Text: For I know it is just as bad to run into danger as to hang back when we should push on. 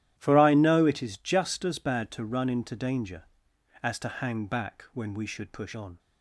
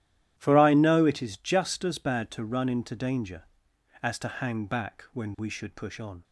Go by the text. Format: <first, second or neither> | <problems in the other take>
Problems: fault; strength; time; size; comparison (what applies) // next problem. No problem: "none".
neither | starts louder than the rest; strong; the same in both